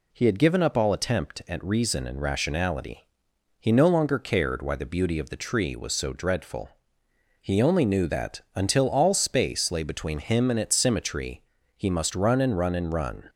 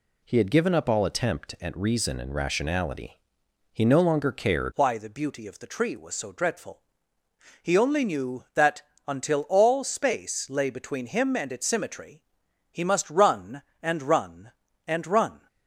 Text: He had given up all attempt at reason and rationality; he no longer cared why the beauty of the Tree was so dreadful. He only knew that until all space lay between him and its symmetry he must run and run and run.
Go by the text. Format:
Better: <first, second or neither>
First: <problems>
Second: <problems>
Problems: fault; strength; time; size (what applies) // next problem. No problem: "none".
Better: first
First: pauses between "symmetry" and "he"; slight; at 11.4 s; 0.34 s long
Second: changes voice at "why"; from 4.7 s on; 10.7 s long // pauses between "that" and "until"; slight; at 8.8 s; 0.24 s long // pauses between "symmetry" and "he"; noticeable; at 12.2 s; 0.48 s long